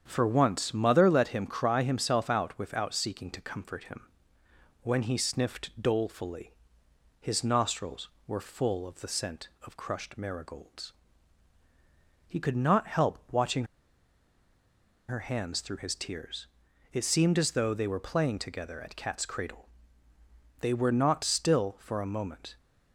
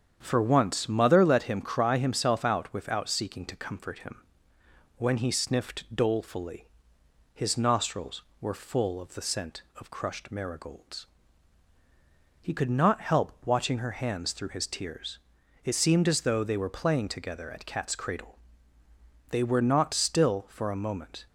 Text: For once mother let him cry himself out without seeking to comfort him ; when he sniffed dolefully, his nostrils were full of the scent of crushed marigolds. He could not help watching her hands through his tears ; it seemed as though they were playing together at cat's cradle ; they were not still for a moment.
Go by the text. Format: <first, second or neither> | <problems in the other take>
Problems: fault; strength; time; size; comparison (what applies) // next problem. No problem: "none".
second | starts louder than the rest; strong; until 1.0 s; 8 dB; strong in the second // pauses between "watching" and "her"; strong; at 13.6 s; 1.4 s long